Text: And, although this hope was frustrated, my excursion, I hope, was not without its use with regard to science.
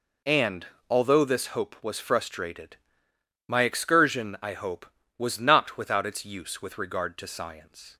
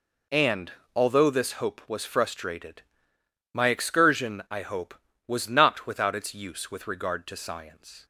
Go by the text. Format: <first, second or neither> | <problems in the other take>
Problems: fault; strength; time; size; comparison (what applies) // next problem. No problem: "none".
neither | none